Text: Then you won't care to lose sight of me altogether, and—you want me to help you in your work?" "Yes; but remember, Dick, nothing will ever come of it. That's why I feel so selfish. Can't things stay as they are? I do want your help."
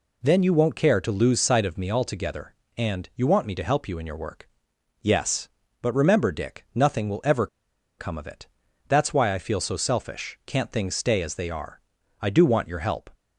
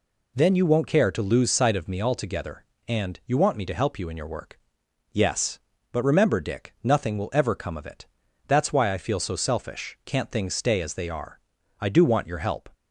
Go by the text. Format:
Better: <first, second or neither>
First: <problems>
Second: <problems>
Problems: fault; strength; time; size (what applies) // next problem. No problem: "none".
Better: second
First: pauses between "ever" and "come"; noticeable; at 7.4 s; 0.51 s long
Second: none